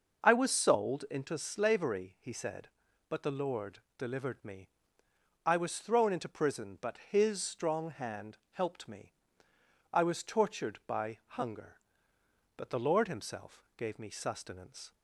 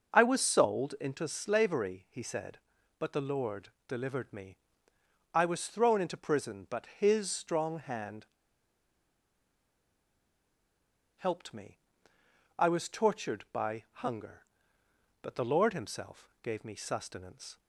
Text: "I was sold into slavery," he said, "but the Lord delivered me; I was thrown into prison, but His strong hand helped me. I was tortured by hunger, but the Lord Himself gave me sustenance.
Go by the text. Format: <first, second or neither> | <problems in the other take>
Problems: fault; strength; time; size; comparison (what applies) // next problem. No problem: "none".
first | pauses between "Lord" and "delivered"; slight; at 3.6 s; 0.18 s long; slight in the first // pauses between "hand" and "helped"; strong; at 8.2 s; 2.9 s long